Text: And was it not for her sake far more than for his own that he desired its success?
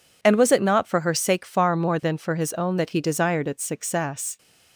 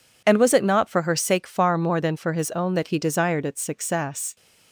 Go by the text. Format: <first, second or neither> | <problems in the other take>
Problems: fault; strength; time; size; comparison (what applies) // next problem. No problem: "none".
neither | none